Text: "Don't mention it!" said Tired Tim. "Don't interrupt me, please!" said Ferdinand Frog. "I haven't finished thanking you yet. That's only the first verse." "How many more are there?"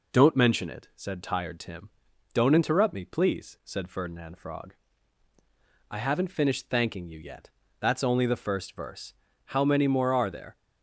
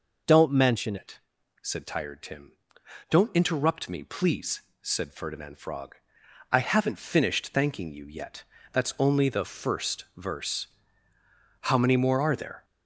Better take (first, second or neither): first